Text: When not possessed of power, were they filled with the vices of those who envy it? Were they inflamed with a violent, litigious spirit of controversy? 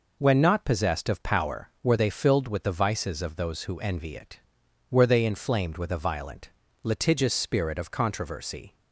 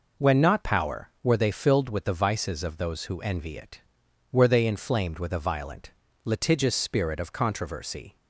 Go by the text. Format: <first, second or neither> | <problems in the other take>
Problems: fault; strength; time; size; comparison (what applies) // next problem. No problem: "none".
first | skips "possessed of"; at 0.6 s